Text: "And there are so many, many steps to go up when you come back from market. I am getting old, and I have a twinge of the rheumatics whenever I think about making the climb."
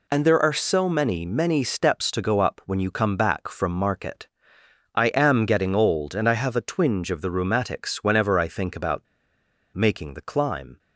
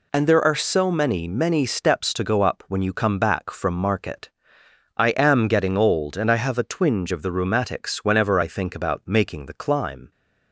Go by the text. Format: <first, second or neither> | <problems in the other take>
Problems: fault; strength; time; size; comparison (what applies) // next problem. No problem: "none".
second | pauses between "about" and "making"; noticeable; at 9.0 s; 0.69 s long